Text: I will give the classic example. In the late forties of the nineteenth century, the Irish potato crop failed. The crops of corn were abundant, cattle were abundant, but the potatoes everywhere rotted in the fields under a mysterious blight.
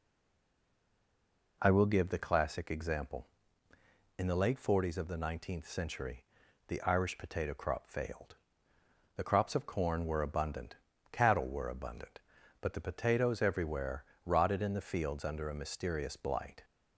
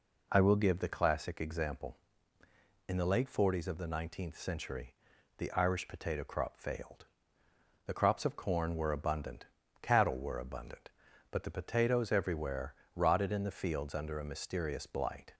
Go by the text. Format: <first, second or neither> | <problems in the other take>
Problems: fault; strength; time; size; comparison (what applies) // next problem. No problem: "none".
second | stays silent before the first word; noticeable; until 1.6 s; 1.6 s long // pauses between "everywhere" and "rotted"; slight; at 14.0 s; 0.20 s long; slight in the second